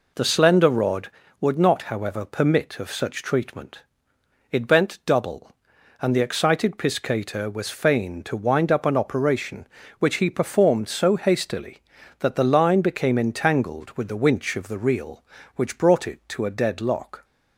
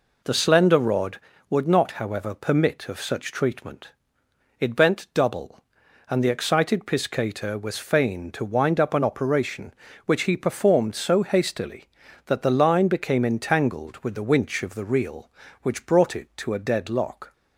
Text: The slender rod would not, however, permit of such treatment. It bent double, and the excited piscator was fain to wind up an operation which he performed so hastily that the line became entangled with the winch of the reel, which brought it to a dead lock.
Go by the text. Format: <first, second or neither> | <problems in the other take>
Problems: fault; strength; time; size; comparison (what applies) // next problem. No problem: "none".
neither | none